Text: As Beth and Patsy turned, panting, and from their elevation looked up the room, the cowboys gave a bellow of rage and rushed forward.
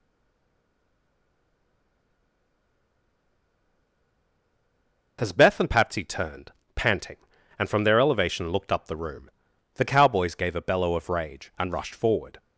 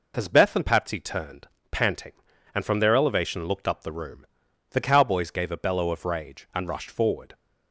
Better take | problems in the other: second | stays silent before the first word; strong; until 5.1 s; 5.1 s long

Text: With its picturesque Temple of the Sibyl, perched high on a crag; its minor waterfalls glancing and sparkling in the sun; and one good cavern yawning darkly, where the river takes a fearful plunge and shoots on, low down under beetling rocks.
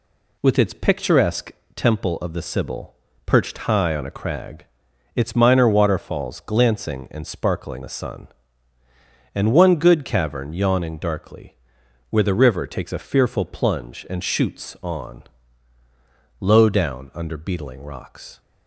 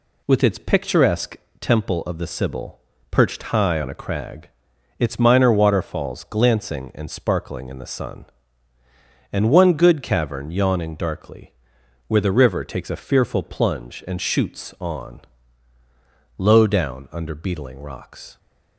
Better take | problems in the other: second | pauses between "picturesque" and "Temple"; slight; at 1.4 s; 0.24 s long; slight in the second // skips "in"; at 7.8 s

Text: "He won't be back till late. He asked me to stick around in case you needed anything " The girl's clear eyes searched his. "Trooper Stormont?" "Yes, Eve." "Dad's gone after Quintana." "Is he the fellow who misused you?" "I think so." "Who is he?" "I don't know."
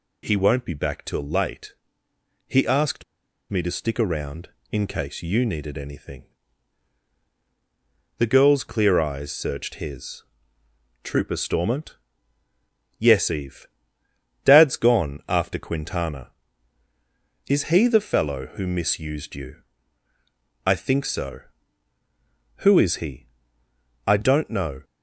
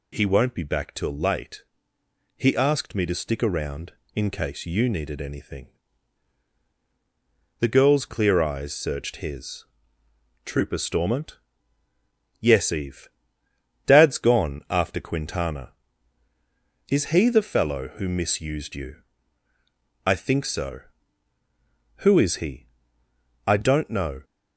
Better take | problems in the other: second | pauses between "asked" and "me"; noticeable; at 3.0 s; 0.46 s long

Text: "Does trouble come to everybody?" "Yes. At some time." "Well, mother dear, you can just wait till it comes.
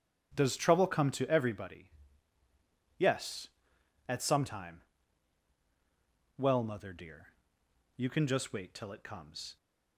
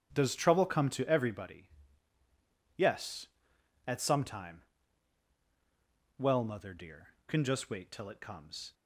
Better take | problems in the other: first | starts louder than the rest; strong; until 1.1 s; 9.5 dB; strong in the first // skips "you"; at 7.2 s

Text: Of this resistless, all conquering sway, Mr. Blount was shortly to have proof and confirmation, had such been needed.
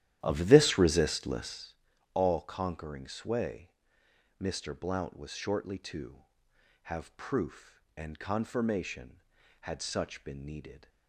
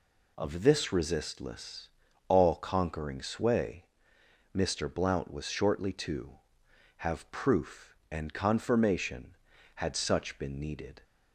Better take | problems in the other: second | starts louder than the rest; strong; until 1.7 s; 12 dB

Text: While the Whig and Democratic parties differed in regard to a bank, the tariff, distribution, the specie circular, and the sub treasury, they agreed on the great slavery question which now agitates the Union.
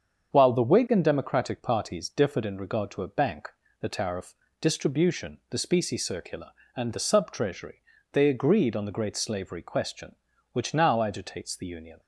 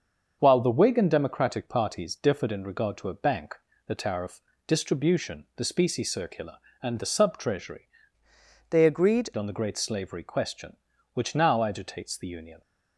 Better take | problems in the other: first | starts louder than the rest; until 1.4 s; 6.5 dB; strong in the first // changes voice from "they" to "agreed"; from 8.6 to 9.2 s; 0.6 s long

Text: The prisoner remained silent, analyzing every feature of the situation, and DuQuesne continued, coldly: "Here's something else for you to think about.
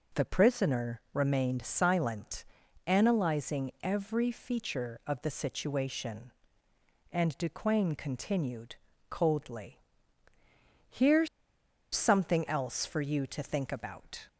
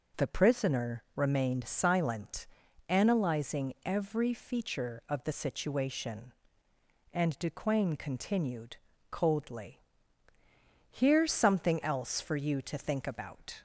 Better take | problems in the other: second | pauses between "Here's" and "something"; noticeable; at 11.2 s; 0.67 s long

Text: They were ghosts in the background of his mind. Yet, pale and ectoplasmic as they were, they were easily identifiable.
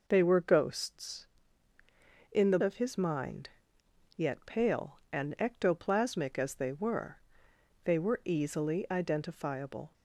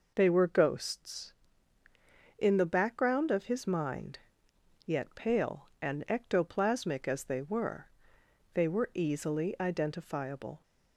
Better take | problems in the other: second | skips "background"; at 2.5 s

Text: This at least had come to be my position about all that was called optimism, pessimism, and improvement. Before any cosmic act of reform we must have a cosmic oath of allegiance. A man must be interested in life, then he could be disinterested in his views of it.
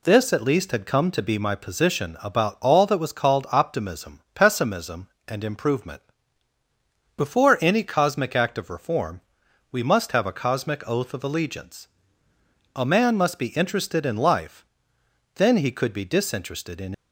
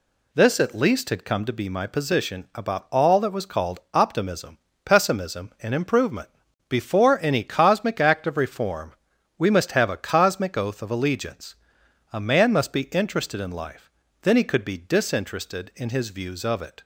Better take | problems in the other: second | pauses between "reform" and "we"; noticeable; at 9.2 s; 0.50 s long; also in the second // stops before "his views of it"; at 16.9 s

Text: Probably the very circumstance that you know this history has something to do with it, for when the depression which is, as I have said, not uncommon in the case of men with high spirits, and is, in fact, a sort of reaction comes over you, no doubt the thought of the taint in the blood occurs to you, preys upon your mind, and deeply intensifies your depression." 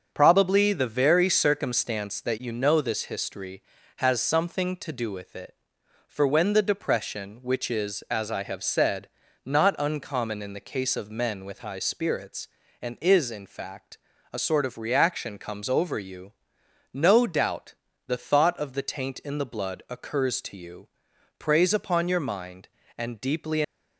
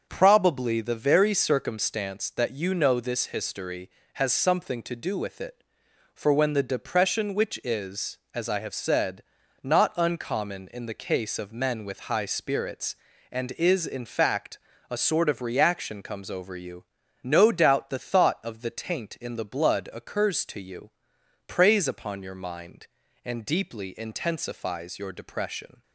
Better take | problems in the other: second | starts louder than the rest; until 1.1 s; 7 dB; also in the second // pauses between "doubt" and "the"; slight; at 17.7 s; 0.32 s long // stops before "intensifies your depression"; at 23.6 s

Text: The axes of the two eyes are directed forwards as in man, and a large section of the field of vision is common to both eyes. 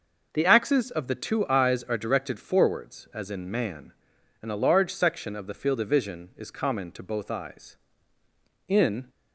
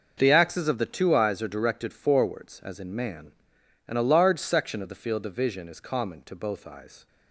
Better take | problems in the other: second | goes on to say "In"; slight; from 8.6 s on; 0.42 s long

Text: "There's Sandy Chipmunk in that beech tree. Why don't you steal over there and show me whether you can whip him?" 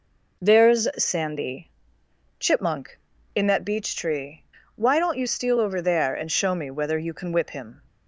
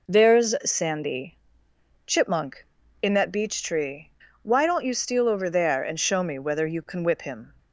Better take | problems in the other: neither | pauses between "Sandy" and "Chipmunk"; noticeable; the same in both

